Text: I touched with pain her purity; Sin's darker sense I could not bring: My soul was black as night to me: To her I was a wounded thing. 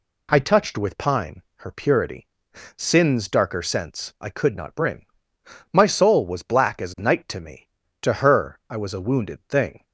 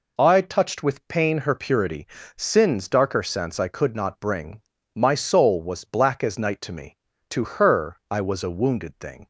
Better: second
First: says "pine" for "pain"; at 0.9 s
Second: none

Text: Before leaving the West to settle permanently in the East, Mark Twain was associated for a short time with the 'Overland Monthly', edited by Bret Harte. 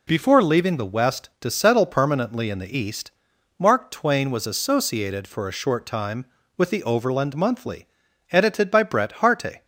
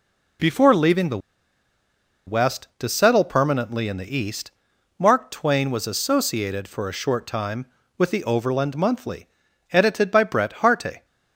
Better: first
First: none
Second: pauses between "the" and "West"; at 1.1 s; 1.0 s long

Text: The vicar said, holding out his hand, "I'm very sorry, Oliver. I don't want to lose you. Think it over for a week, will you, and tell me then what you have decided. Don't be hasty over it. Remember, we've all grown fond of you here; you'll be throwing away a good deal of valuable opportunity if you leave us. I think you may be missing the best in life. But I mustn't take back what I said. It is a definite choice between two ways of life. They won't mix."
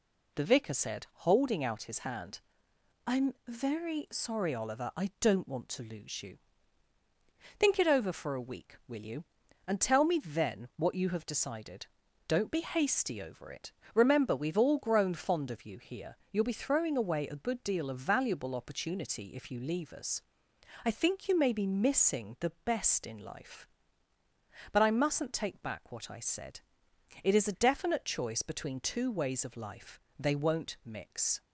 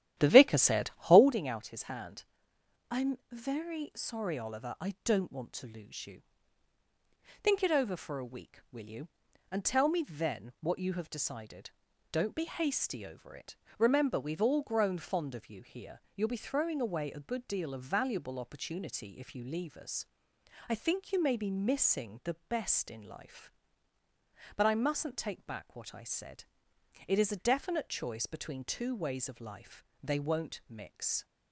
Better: first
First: none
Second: starts louder than the rest; strong; until 1.4 s; 11.5 dB

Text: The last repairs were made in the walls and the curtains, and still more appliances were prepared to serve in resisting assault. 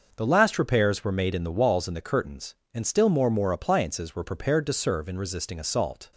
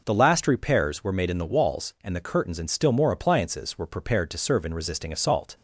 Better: second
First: starts louder than the rest; noticeable; until 1.1 s; 6 dB // says "more" twice; at 3.2 s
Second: none

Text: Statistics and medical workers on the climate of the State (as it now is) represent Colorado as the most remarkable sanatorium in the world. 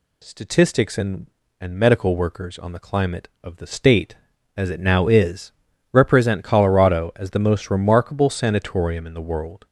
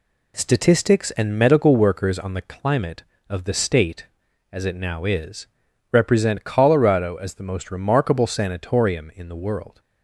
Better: second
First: says "and" twice; at 1.5 s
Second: none

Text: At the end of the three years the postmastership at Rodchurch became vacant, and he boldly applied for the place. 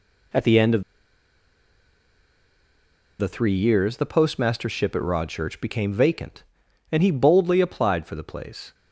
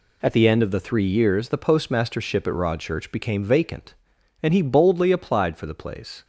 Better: second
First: pauses between "of" and "the"; strong; at 0.8 s; 2.3 s long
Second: none

